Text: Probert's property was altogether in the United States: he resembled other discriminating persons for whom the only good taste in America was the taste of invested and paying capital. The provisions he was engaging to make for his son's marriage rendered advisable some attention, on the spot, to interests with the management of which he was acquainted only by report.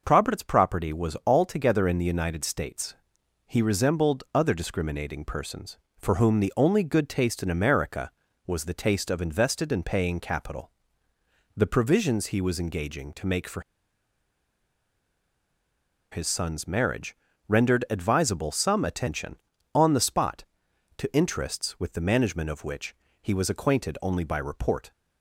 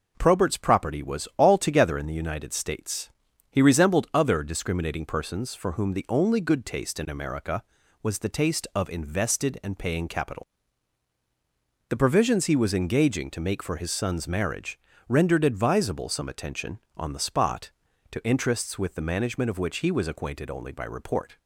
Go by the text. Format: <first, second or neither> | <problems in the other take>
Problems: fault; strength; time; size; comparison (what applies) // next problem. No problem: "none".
second | pauses between "for" and "his"; strong; at 13.6 s; 2.5 s long // pauses between "marriage" and "rendered"; slight; at 17.1 s; 0.32 s long; slight in the second // pauses between "which" and "he"; slight; at 22.9 s; 0.30 s long